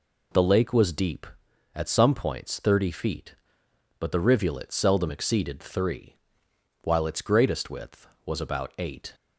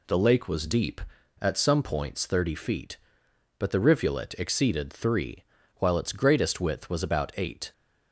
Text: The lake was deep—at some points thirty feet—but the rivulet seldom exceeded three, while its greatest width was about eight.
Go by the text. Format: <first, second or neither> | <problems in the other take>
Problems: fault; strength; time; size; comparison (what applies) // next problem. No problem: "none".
first | skips "seldom"; at 4.3 s